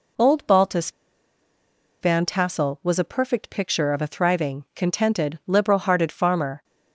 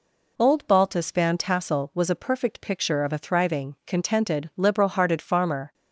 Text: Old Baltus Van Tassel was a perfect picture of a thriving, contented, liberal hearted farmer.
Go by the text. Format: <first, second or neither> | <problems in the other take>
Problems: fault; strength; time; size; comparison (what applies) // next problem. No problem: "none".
second | pauses between "Baltus" and "Van"; at 0.9 s; 1.1 s long